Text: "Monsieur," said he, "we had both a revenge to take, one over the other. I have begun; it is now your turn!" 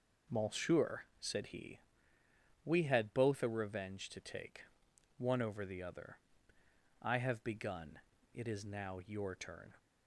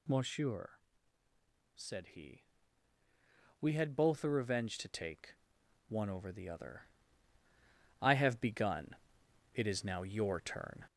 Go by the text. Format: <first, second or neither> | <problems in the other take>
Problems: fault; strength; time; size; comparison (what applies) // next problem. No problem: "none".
first | gets louder; slight; throughout; 3 dB